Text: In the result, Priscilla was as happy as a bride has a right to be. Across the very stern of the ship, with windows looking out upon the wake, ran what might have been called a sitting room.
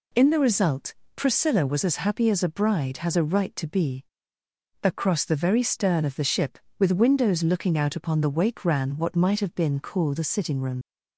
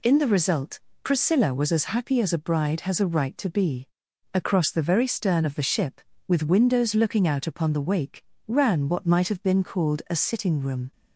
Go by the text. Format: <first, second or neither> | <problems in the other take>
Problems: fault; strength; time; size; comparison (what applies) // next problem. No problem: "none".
second | leaves "room" unfinished; at 10.8 s; 65 ms